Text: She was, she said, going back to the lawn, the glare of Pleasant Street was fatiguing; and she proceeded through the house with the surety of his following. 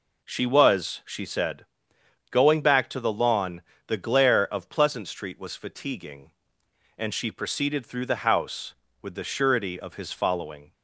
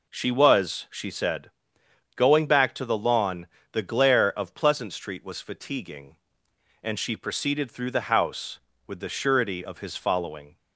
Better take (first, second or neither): neither